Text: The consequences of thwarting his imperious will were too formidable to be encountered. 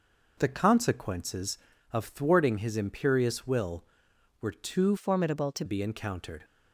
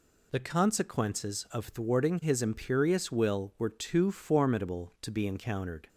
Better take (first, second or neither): second